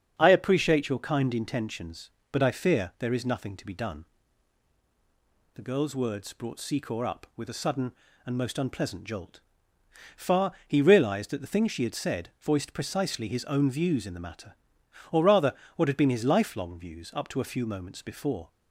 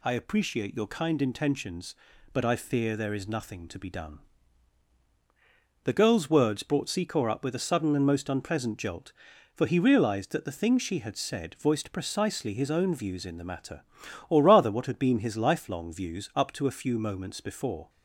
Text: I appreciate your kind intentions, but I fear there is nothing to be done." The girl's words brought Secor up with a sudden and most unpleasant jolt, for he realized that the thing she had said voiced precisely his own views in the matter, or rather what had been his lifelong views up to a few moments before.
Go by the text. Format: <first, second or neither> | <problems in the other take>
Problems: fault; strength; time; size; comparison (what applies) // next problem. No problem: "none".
second | starts louder than the rest; until 1.1 s; 7 dB // says "far" for "for"; at 10.1 s // pauses between "rather" and "what"; slight; at 15.5 s; 0.22 s long